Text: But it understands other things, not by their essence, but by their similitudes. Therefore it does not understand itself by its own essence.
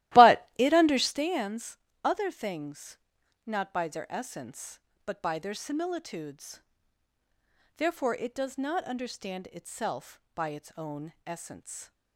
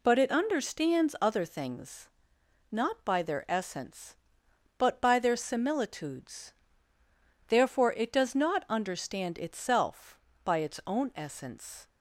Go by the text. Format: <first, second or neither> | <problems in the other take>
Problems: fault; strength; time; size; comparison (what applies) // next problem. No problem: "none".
second | starts louder than the rest; strong; until 1.3 s; 15.5 dB // pauses between "understands" and "other"; slight; at 1.7 s; 0.26 s long